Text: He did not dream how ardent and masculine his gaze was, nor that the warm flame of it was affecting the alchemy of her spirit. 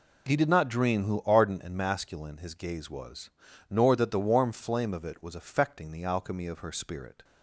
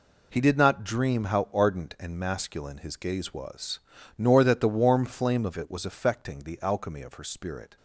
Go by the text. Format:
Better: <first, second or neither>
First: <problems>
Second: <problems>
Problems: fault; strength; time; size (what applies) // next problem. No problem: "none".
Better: second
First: says "who" for "how"; at 1.0 s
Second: none